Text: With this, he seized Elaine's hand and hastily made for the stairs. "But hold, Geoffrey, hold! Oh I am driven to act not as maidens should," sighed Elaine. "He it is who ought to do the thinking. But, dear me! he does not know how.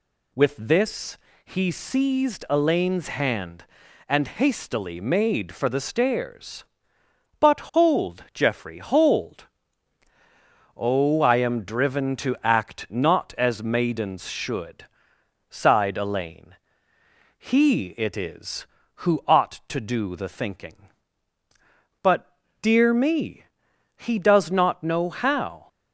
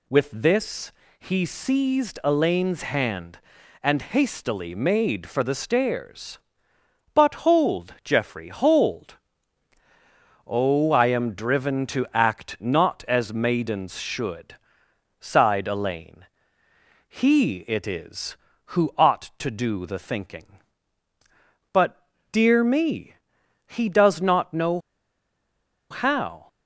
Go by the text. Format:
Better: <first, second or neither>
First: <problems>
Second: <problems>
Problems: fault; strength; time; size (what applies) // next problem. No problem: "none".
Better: first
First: none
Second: pauses between "know" and "how"; at 24.7 s; 1.1 s long